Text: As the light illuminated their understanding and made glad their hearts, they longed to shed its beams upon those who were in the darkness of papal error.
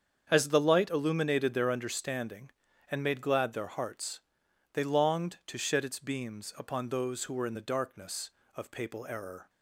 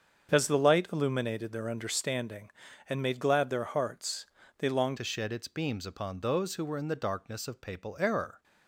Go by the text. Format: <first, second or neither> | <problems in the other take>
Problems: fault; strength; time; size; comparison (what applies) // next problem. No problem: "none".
first | starts louder than the rest; until 1.3 s; 7 dB; strong in the first // changes voice at "to"; from 4.9 s on; 3.5 s long